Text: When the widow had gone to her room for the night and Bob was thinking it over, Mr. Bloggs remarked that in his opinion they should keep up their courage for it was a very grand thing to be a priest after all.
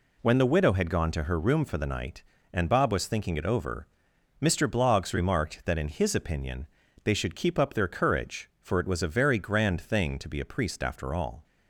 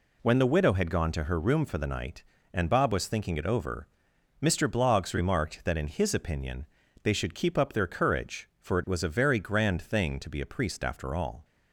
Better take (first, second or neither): neither